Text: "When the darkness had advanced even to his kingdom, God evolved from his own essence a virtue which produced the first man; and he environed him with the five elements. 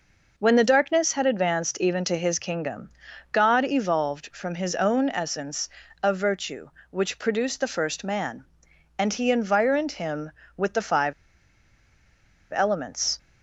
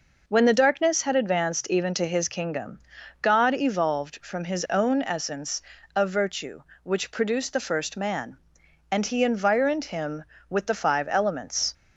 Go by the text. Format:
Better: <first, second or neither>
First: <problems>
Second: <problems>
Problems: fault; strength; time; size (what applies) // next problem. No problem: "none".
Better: second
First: pauses between "essence" and "a"; slight; at 5.6 s; 0.36 s long // pauses between "five" and "elements"; strong; at 11.1 s; 1.4 s long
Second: pauses between "essence" and "a"; slight; at 5.5 s; 0.36 s long